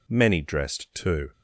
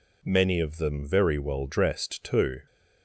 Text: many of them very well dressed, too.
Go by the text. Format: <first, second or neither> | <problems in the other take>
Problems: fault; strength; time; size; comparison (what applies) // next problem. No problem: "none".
second | skips "of them very well"; at 0.4 s